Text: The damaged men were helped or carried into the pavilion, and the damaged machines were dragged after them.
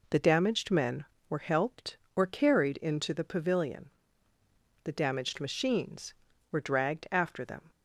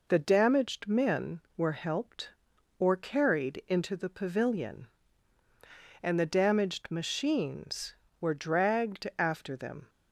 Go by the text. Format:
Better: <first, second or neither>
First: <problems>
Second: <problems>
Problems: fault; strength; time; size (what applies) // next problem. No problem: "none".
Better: second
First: skips "and"; at 4.3 s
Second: none